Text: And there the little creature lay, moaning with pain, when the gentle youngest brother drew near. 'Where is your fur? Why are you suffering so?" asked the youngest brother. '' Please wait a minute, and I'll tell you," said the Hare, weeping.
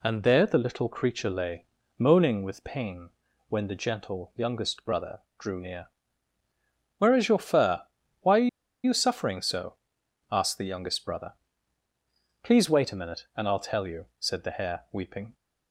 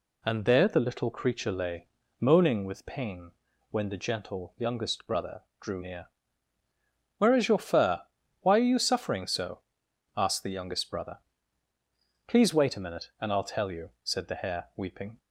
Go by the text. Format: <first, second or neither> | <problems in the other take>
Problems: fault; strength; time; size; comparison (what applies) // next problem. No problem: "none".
second | pauses between "brother" and "drew"; slight; at 5.2 s; 0.18 s long; slight in the second // pauses between "are" and "you"; at 8.4 s; 0.37 s long